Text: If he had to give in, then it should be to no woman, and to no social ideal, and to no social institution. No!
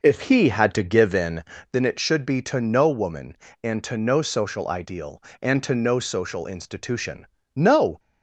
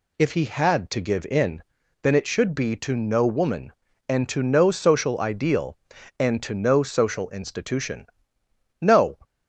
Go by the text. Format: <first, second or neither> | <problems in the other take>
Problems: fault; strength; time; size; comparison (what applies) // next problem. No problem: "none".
second | starts louder than the rest; noticeable; until 1.8 s; 5 dB